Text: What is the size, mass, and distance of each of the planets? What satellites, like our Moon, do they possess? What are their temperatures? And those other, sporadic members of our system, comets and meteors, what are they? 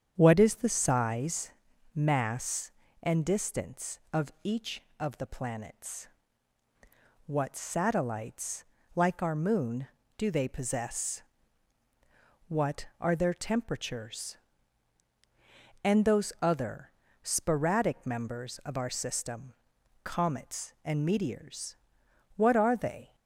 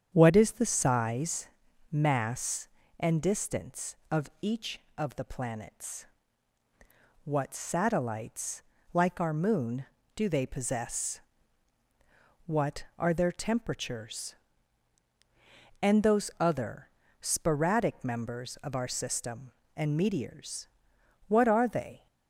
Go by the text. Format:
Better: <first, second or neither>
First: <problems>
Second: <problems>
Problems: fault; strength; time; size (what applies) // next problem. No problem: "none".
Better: first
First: starts louder than the rest; strong; until 1.1 s; 8 dB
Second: starts louder than the rest; strong; until 1.1 s; 8 dB // skips "comets"; at 19.6 s